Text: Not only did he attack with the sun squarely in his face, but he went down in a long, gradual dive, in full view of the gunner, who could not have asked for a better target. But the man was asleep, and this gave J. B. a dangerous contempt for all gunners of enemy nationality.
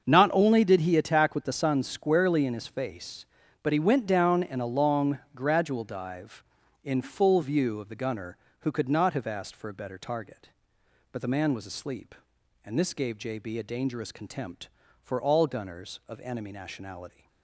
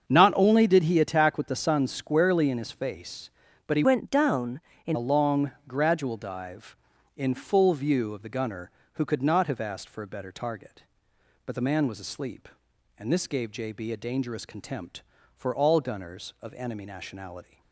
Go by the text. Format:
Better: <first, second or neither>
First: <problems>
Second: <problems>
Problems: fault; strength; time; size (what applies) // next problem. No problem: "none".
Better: first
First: starts louder than the rest; until 1.1 s; 6.5 dB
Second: starts louder than the rest; until 1.1 s; 7 dB // changes voice from "went" to "in"; from 3.8 to 4.9 s; 1.1 s long